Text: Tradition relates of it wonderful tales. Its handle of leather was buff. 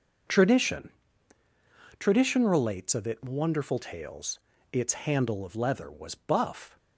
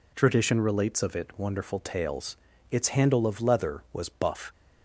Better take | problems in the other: second | says "Tradition" twice; at 1.9 s

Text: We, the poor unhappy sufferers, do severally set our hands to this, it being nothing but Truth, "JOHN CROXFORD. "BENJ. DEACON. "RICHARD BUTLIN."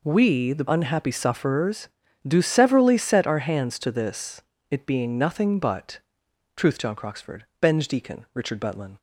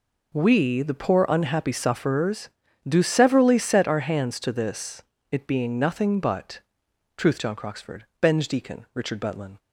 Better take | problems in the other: second | skips "poor"; at 0.6 s // pauses between "but" and "Truth"; noticeable; at 5.9 s; 0.56 s long; noticeable in the second

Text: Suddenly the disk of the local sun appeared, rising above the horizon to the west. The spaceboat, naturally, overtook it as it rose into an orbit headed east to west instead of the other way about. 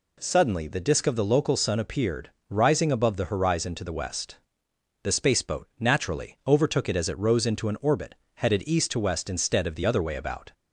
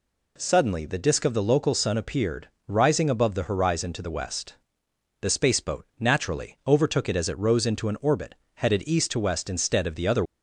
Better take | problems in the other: first | pauses between "orbit" and "headed"; slight; at 8.3 s; 0.20 s long; slight in the first // stops before "way about"; at 10.2 s

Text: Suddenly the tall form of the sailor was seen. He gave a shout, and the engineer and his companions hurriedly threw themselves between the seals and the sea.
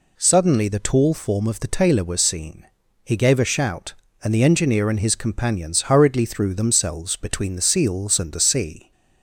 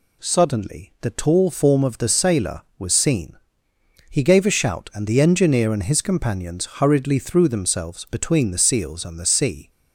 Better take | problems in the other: second | says "tailor" for "sailor"; at 1.6 s

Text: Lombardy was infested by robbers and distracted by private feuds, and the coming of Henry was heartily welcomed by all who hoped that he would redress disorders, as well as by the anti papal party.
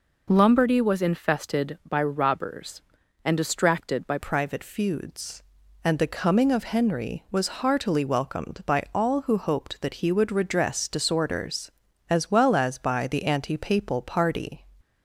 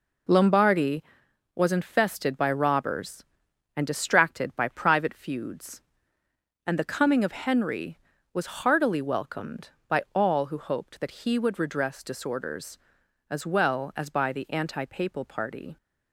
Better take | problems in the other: second | changes voice at "private"; from 4.1 s on; 10.5 s long

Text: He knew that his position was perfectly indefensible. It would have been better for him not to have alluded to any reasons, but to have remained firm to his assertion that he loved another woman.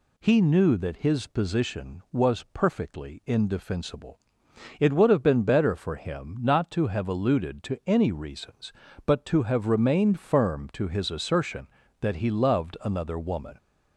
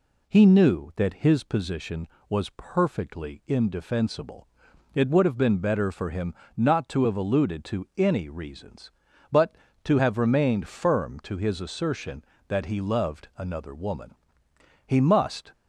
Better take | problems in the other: first | pauses between "him" and "not"; slight; at 6.3 s; 0.22 s long // goes on to say "He must"; noticeable; from 14.8 s on; 0.66 s long

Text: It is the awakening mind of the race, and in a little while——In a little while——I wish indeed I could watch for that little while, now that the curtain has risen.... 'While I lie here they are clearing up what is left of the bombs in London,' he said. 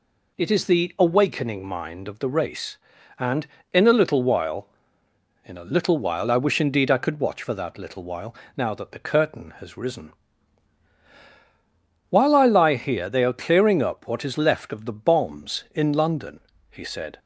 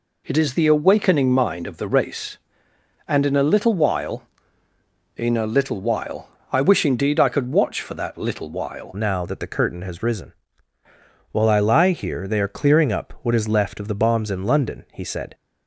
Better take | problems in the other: first | changes voice at "now"; from 8.9 s on; 6.4 s long

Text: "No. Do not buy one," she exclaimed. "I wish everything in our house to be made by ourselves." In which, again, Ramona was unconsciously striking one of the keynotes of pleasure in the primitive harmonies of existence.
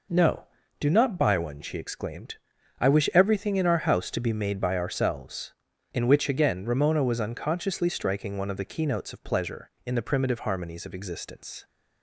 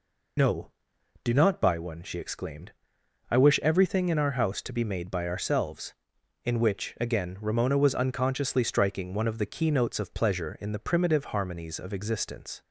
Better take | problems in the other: first | loses the start of "No"; at 0.3 s; 60 ms

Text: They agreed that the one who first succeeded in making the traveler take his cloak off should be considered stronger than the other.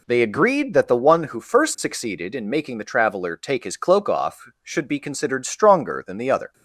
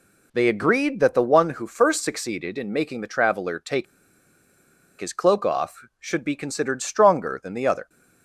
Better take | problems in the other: first | pauses between "take" and "his"; at 3.8 s; 1.1 s long

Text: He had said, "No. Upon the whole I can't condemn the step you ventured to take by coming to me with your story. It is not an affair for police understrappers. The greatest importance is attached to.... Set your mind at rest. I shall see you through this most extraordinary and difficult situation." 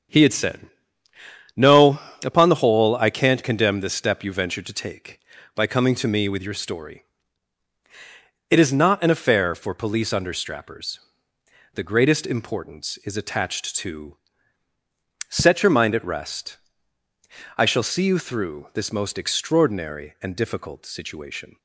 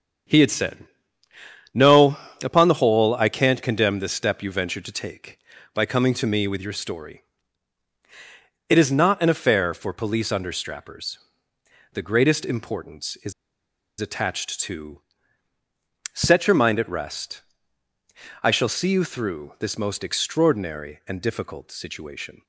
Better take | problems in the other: first | starts louder than the rest; strong; until 2.1 s; 7.5 dB; strong in the first // pauses between "is" and "attached"; noticeable; at 13.3 s; 0.68 s long

